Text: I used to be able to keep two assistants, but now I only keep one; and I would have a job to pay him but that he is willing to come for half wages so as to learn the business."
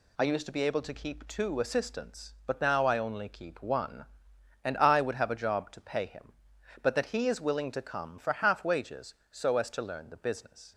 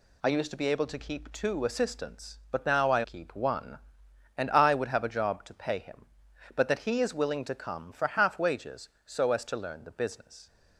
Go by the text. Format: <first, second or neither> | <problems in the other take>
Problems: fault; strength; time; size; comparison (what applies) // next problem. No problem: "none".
first | skips "only"; at 3.0 s